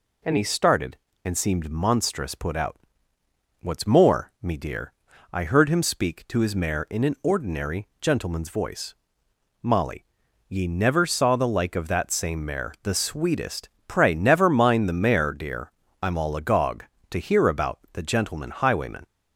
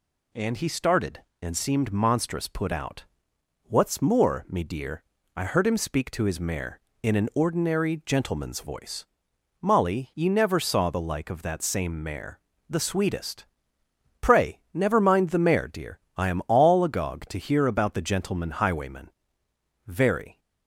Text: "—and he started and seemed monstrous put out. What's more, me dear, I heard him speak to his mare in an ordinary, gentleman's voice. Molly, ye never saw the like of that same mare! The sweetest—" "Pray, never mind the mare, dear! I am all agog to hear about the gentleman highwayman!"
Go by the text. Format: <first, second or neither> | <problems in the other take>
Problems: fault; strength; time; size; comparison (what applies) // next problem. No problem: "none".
first | goes on to say "Very"; from 19.8 s on; 0.52 s long